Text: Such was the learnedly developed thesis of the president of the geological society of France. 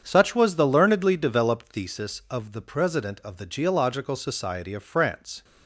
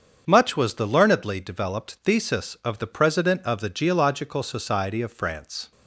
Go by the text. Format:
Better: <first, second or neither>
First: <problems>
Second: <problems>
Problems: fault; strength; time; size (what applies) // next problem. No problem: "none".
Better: first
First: starts louder than the rest; strong; until 1.0 s; 7.5 dB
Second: starts louder than the rest; until 1.2 s; 7 dB // says "Much" for "Such"; at 0.2 s